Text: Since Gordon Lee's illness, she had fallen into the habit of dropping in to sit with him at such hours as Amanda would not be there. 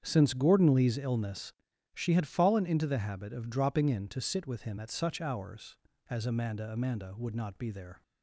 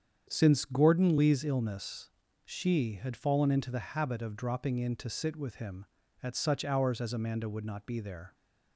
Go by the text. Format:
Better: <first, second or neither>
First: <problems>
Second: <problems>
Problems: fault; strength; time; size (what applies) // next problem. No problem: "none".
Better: second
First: starts louder than the rest; strong; until 1.0 s; 8 dB // says "Amanda" twice; at 6.7 s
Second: starts louder than the rest; strong; until 1.3 s; 8 dB